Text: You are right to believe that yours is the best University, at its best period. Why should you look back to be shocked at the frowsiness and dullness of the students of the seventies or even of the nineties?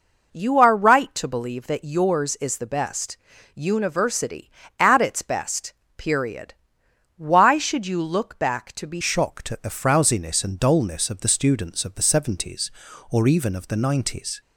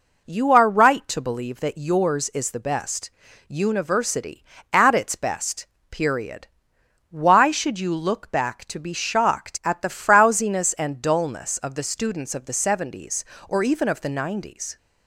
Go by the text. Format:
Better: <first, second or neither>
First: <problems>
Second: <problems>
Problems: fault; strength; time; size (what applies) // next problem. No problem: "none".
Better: second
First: pauses between "best" and "University"; at 3.1 s; 0.38 s long // pauses between "best" and "period"; slight; at 5.7 s; 0.24 s long // changes voice at "shocked"; from 9.0 s on; 5.4 s long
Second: pauses between "best" and "University"; at 3.0 s; 0.38 s long // pauses between "best" and "period"; slight; at 5.6 s; 0.24 s long